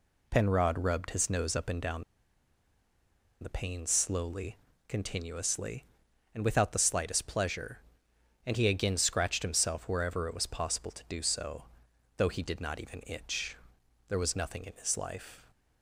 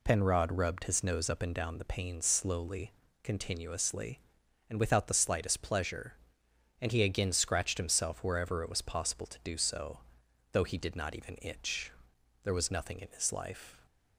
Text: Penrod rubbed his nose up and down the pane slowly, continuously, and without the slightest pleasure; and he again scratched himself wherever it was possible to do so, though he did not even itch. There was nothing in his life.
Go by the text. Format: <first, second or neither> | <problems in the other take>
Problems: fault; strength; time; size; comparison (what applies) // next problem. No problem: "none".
second | pauses between "down" and "the"; strong; at 2.0 s; 1.3 s long